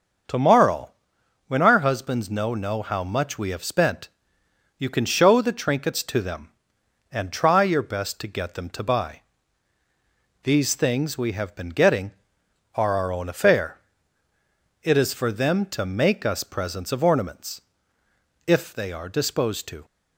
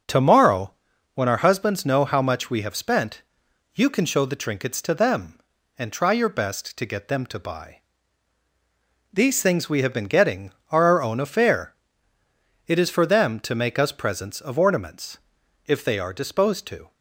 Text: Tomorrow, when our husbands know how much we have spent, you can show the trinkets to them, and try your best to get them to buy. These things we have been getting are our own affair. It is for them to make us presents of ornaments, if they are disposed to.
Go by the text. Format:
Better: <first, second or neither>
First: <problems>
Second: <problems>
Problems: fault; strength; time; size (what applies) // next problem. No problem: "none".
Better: second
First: starts louder than the rest; until 1.8 s; 6.5 dB // says "know" twice; at 2.5 s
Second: starts louder than the rest; noticeable; until 1.4 s; 6 dB